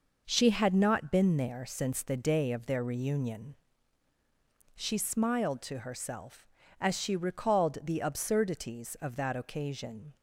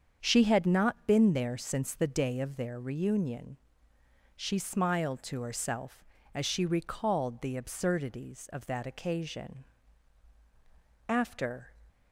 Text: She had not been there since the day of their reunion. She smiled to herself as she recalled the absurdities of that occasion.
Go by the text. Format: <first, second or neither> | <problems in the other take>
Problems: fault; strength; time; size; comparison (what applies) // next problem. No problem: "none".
first | starts louder than the rest; strong; until 1.2 s; 7 dB // goes on to say "After"; noticeable; from 11.0 s on; 0.62 s long